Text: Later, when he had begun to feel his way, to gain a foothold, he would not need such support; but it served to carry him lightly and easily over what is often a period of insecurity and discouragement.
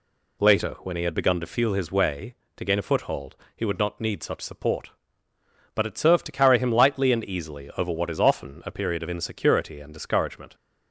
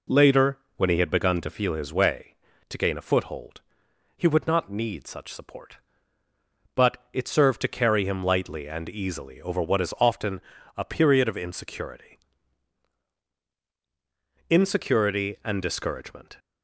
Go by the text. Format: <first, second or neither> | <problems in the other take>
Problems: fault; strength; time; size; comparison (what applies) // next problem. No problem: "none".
first | pauses between "but" and "it"; slight; at 6.9 s; 0.16 s long // pauses between "often" and "a"; at 10.4 s; 0.38 s long // says "insecurity" twice; at 14.4 s